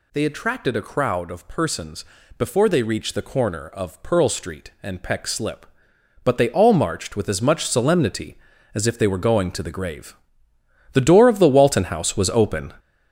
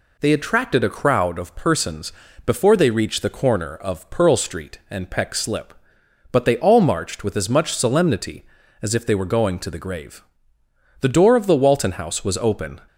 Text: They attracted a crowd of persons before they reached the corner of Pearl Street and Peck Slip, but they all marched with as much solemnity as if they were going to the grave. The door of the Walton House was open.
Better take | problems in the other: second | gets louder; strong; throughout; 7.5 dB // pauses between "persons" and "before"; slight; at 2.0 s; 0.34 s long; slight in the second

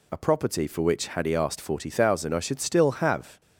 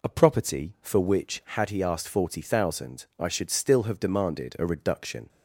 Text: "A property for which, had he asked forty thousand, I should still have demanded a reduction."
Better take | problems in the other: second | stops before "demanded a reduction"; at 3.4 s

